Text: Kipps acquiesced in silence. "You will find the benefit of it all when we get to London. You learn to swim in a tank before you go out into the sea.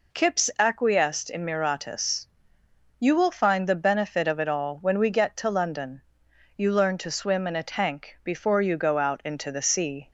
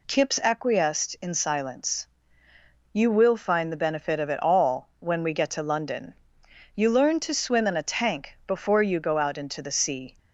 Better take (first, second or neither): second